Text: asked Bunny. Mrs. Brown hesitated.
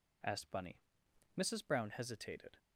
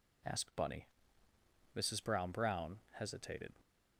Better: first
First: none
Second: says "Brown" twice; at 2.2 s

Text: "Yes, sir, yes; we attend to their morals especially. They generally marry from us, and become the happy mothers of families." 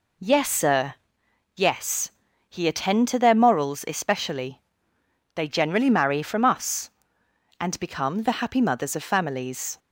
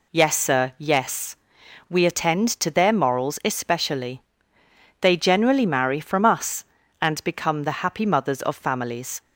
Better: second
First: says "he" for "we"; at 2.4 s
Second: none

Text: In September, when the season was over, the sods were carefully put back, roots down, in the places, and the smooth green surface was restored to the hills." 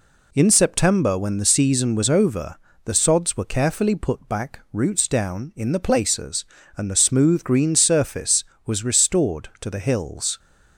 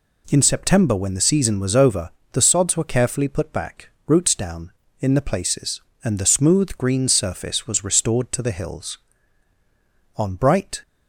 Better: first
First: none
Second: goes on to say "On bright"; noticeable; from 10.1 s on; 0.66 s long

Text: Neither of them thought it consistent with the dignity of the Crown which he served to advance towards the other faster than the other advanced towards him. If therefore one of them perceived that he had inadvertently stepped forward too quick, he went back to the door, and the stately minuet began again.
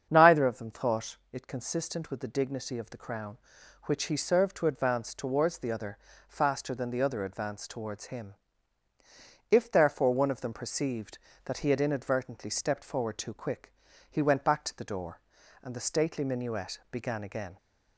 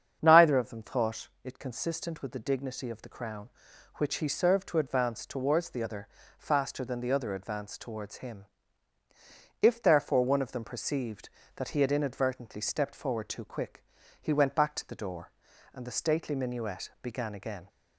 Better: neither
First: starts louder than the rest; strong; until 1.1 s; 7.5 dB // pauses between "thought" and "it"; slight; at 1.1 s; 0.16 s long // pauses between "other" and "faster"; slight; at 5.9 s; 0.32 s long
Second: starts louder than the rest; strong; until 1.2 s; 7.5 dB // pauses between "thought" and "it"; slight; at 1.2 s; 0.16 s long // pauses between "other" and "faster"; slight; at 6.0 s; 0.32 s long

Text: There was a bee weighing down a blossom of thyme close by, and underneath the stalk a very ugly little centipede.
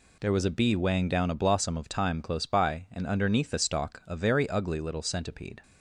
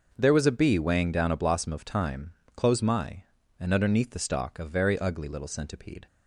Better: first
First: none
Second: starts louder than the rest; until 1.1 s; 6.5 dB // pauses between "thyme" and "close"; slight; at 2.3 s; 0.22 s long // says "my" for "by"; at 2.8 s

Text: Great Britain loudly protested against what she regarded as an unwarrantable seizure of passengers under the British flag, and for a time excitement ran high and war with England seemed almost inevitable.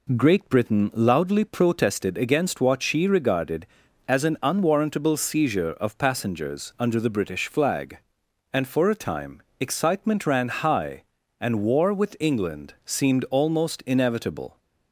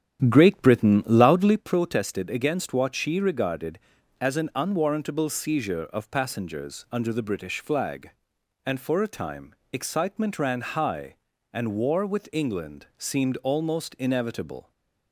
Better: first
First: pauses between "time" and "excitement"; slight; at 9.4 s; 0.18 s long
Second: starts louder than the rest; strong; until 1.6 s; 10 dB // pauses between "time" and "excitement"; slight; at 9.5 s; 0.18 s long

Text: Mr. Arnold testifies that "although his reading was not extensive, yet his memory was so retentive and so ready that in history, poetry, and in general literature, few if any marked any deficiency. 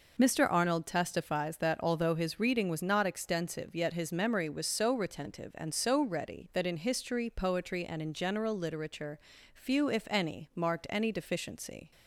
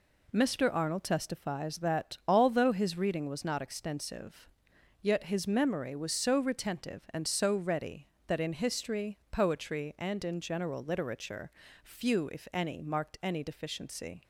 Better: neither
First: none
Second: none

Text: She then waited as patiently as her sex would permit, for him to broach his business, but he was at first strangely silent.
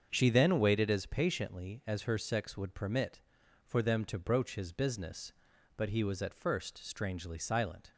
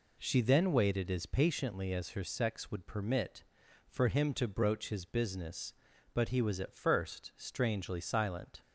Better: second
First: starts louder than the rest; until 1.1 s; 7 dB // says "them" for "him"; at 3.8 s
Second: none

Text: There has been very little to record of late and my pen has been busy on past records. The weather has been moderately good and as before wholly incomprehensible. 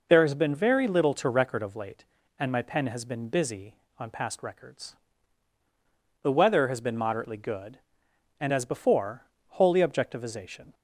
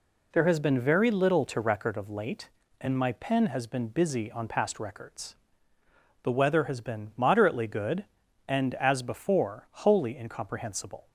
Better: second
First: pauses between "before" and "wholly"; slight; at 9.2 s; 0.22 s long // says "objectivization" for "incomprehensible"; at 9.7 s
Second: none

